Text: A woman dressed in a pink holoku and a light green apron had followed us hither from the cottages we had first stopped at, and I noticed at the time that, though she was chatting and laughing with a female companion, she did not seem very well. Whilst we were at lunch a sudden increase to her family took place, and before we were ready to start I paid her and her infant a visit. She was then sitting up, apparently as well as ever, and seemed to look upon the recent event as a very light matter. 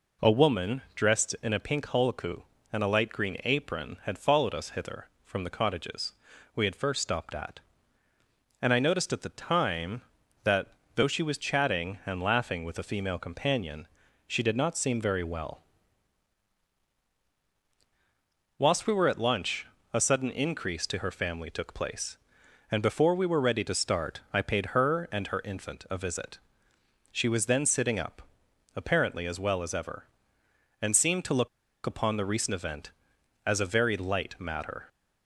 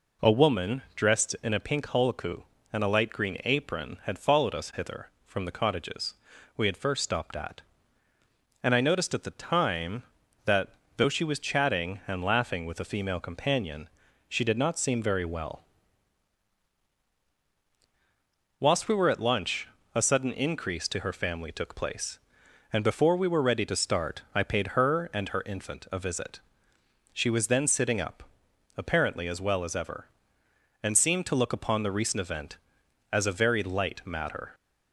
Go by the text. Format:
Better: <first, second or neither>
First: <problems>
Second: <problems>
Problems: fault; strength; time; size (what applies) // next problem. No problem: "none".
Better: second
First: pauses between "woman" and "dressed"; slight; at 0.8 s; 0.16 s long // pauses between "cottages" and "we"; at 6.1 s; 0.44 s long // pauses between "lunch" and "a"; slight; at 19.6 s; 0.26 s long // pauses between "look" and "upon"; at 31.4 s; 0.37 s long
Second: pauses between "woman" and "dressed"; slight; at 0.8 s; 0.16 s long // pauses between "cottages" and "we"; at 6.1 s; 0.44 s long // pauses between "lunch" and "a"; slight; at 19.6 s; 0.26 s long